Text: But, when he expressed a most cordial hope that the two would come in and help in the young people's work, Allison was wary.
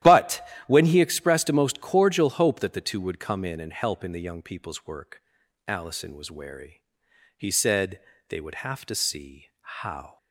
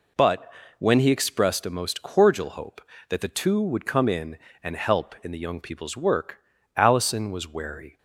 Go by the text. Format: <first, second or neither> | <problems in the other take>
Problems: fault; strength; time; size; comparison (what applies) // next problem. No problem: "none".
second | starts louder than the rest; strong; until 1.2 s; 12 dB // goes on to say "He said they would have to see how"; strong; from 7.3 s on; 2.8 s long